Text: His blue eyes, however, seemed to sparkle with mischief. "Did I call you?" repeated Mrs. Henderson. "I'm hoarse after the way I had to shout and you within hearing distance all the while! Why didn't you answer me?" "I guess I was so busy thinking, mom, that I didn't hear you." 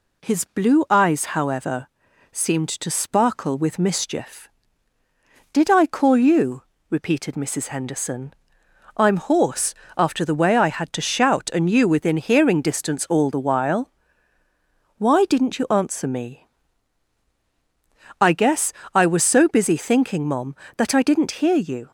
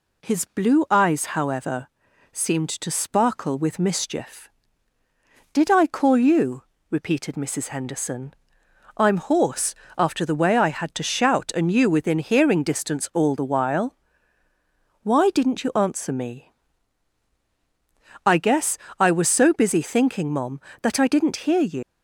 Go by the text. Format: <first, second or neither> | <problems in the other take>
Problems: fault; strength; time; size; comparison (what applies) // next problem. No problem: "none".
first | pauses between "hoarse" and "after"; slight; at 9.7 s; 0.22 s long; slight in the first // pauses between "guess" and "I"; slight; at 18.7 s; 0.20 s long; slight in the first // leaves "you" unfinished; at 21.8 s; 125 ms